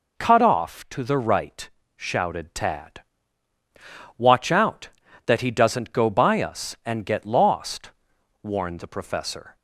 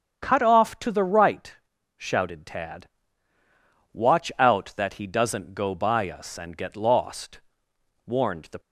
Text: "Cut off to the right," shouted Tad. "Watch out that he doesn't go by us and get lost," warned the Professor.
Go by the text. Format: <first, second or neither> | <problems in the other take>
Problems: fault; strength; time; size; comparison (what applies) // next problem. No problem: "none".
first | starts louder than the rest; strong; until 1.2 s; 7.5 dB // stops before "Professor"; at 8.5 s